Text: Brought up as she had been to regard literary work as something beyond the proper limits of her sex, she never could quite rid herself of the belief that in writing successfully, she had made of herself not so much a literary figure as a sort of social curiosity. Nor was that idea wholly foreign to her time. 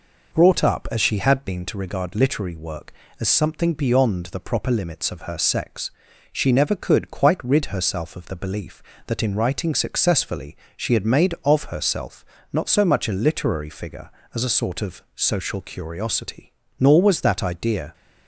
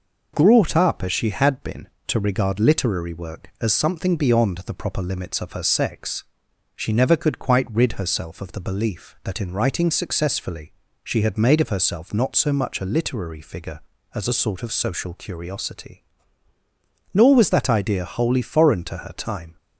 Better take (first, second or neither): second